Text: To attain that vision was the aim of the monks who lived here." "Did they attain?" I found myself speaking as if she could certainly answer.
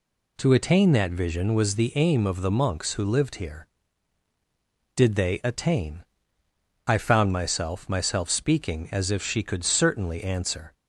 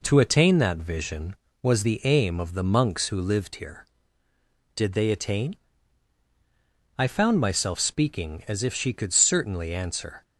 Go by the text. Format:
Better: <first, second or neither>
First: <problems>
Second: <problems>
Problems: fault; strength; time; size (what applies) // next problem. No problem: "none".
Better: second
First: says "myself" twice; at 7.8 s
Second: none